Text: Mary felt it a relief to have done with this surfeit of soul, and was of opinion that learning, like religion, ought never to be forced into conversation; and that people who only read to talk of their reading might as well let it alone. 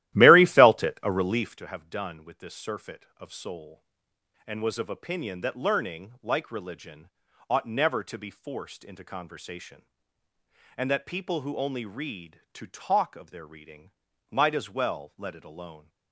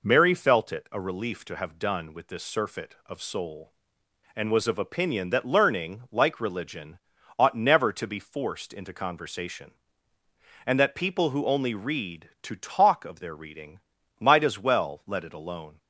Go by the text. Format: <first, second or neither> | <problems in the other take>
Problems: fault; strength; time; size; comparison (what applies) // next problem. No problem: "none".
second | starts louder than the rest; strong; until 1.6 s; 14.5 dB // pauses between "reading" and "might"; at 13.8 s; 0.42 s long; also in the second